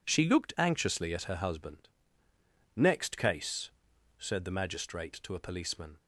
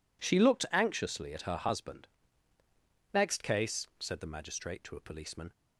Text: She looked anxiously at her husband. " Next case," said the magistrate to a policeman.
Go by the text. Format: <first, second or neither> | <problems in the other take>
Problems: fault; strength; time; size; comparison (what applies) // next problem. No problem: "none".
neither | none